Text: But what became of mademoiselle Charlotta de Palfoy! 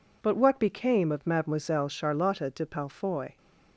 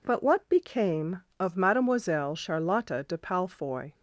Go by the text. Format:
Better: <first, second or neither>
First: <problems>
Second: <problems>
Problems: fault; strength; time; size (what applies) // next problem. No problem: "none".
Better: neither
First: none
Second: none